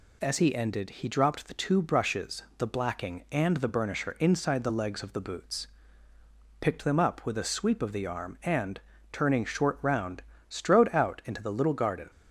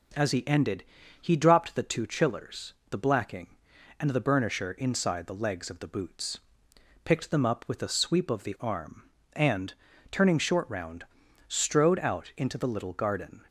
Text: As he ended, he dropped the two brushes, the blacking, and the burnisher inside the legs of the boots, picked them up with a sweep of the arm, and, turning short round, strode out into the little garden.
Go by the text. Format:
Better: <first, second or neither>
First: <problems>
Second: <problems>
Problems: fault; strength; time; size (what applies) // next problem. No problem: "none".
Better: first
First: none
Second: says "chillers" for "brushes"; at 2.0 s